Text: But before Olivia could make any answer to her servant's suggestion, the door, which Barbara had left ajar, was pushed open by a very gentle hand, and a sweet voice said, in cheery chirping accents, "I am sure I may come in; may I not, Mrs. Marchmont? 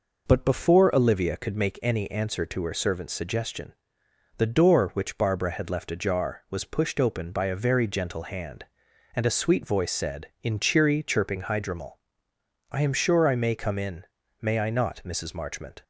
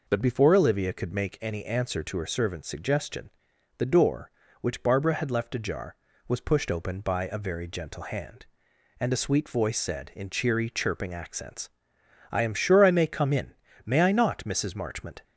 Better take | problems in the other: second | says "hydromel" for "accents"; at 11.4 s

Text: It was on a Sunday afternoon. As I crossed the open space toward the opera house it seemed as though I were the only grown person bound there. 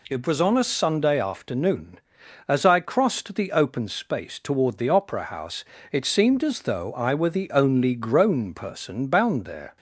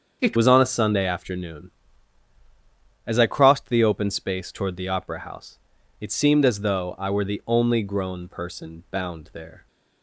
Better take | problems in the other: first | starts louder than the rest; until 1.2 s; 7 dB // changes voice at "was"; from 0.3 s on; 9.3 s long // pauses between "house" and "it"; at 5.5 s; 0.40 s long; slight in the first

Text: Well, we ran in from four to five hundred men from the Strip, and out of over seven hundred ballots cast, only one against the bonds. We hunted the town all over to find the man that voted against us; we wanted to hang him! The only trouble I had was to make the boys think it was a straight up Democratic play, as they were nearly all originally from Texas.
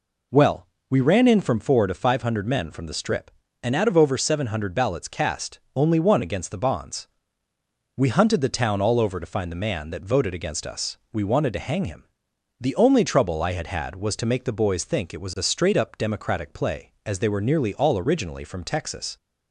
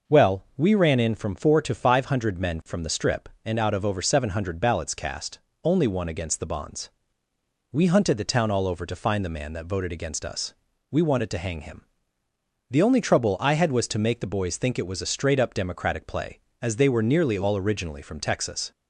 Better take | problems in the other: second | says "had" twice; at 13.6 s

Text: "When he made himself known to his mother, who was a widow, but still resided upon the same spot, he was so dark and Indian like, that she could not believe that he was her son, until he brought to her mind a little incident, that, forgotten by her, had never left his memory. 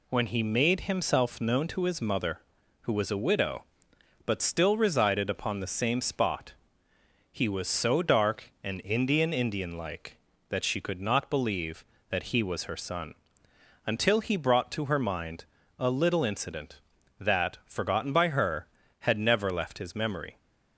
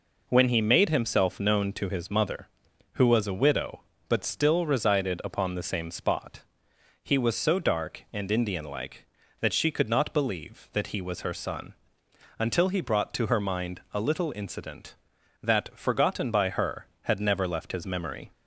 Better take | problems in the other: second | says "Indian" twice; at 9.3 s // pauses between "mind" and "a"; slight; at 15.4 s; 0.34 s long

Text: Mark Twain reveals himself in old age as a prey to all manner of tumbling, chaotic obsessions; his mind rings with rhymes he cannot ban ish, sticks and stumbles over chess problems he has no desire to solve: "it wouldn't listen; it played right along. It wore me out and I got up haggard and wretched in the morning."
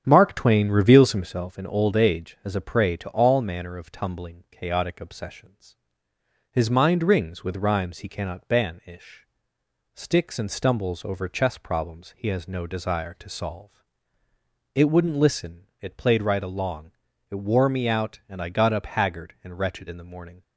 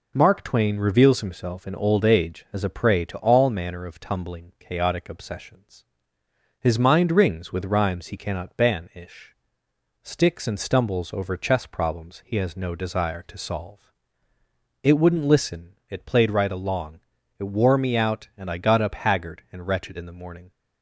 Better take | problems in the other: second | starts louder than the rest; strong; until 1.6 s; 8 dB

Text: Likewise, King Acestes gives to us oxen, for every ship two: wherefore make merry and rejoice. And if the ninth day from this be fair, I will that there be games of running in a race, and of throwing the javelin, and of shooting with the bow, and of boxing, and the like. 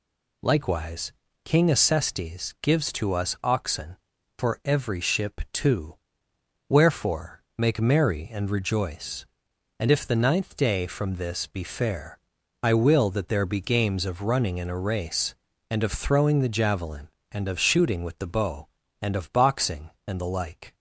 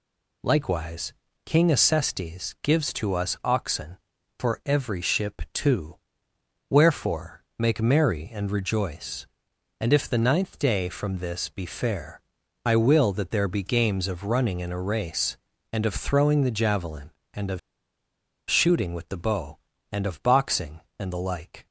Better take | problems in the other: first | pauses between "wherefore" and "make"; slight; at 7.4 s; 0.16 s long; slight in the first // pauses between "of" and "shooting"; noticeable; at 17.5 s; 0.90 s long

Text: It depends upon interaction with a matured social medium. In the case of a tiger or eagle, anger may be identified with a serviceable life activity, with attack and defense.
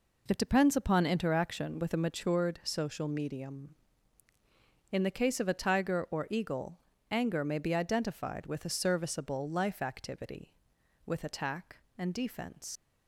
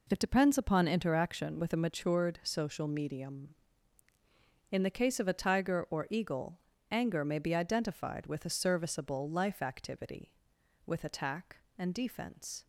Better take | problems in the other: second | leaves "defense" unfinished; at 12.7 s; 105 ms

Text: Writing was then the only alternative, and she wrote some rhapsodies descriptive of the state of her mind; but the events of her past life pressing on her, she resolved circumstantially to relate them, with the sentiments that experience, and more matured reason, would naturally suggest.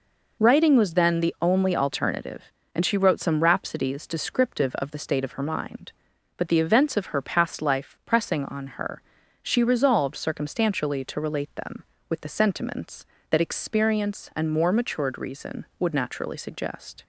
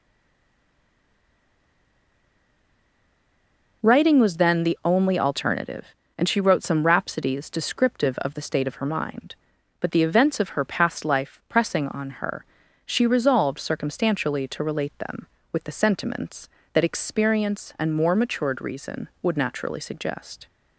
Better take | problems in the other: first | stays silent before the first word; strong; until 3.8 s; 3.8 s long

